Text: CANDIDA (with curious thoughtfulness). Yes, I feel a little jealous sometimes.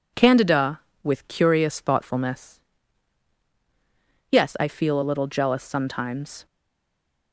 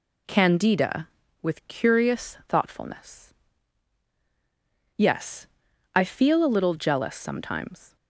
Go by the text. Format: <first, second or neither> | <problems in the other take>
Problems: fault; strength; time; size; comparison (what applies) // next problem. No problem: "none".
second | stays silent after the last word; slight; from 6.4 s on; 0.9 s long